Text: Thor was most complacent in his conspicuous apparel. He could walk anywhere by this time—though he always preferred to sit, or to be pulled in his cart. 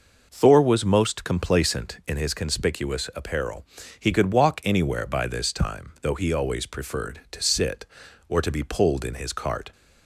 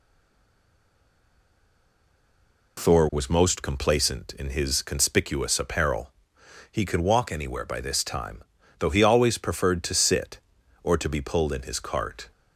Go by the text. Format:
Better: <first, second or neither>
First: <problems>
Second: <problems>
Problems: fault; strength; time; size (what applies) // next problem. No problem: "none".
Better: first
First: none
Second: stays silent before the first word; strong; until 2.7 s; 2.7 s long